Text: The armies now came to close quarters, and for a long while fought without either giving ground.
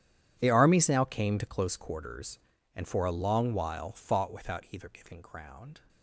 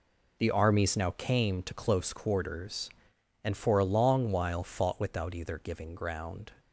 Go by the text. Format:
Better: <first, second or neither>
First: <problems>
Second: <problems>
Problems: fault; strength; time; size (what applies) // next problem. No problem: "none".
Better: second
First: gets quieter; strong; throughout; 18 dB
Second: none